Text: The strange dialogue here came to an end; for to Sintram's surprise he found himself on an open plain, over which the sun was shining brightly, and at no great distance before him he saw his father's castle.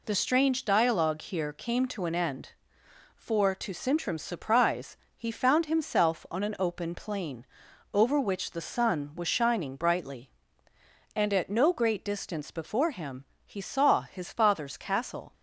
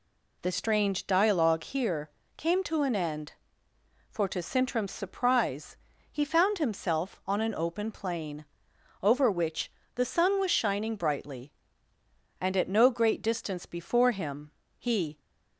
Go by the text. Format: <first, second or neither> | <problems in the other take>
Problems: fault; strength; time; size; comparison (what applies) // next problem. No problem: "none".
first | pauses between "here" and "came"; slight; at 2.1 s; 0.26 s long // pauses between "surprise" and "he"; at 5.7 s; 0.38 s long; slight in the first // pauses between "which" and "the"; slight; at 9.6 s; 0.28 s long // pauses between "him" and "he"; slight; at 14.5 s; 0.26 s long; slight in the first // stops before "saw his father's castle"; at 15.1 s